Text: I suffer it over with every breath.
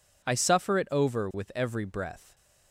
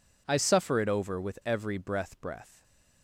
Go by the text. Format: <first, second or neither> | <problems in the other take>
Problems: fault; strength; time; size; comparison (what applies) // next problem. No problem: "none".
first | says "breath" twice; at 2.1 s // stays silent after the last word; slight; from 2.5 s on; 0.5 s long